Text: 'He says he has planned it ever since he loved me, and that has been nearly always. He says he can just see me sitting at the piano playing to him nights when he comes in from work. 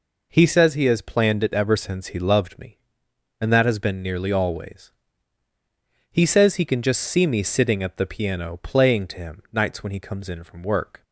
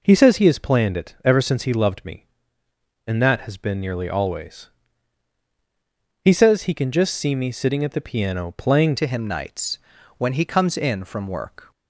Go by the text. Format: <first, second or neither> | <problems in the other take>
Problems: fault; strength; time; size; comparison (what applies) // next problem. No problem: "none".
first | changes voice at "to"; from 8.9 s on; 2.8 s long // pauses between "nights" and "when"; at 9.7 s; 0.40 s long